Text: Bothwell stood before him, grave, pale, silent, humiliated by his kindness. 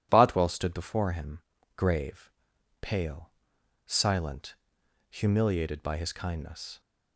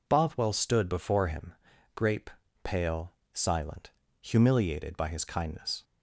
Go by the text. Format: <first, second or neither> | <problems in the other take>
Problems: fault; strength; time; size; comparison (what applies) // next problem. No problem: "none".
first | says "grape" for "grave"; at 1.9 s